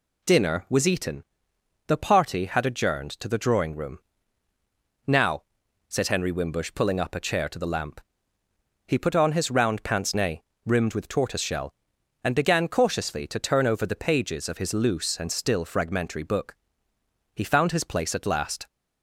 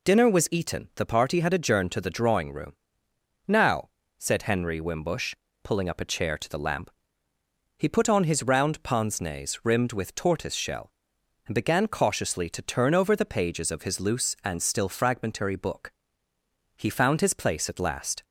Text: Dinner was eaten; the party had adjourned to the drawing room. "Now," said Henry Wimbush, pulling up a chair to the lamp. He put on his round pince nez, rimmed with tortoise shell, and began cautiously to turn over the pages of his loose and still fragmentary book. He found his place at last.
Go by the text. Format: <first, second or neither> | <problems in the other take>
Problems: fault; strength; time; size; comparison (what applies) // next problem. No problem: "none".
neither | none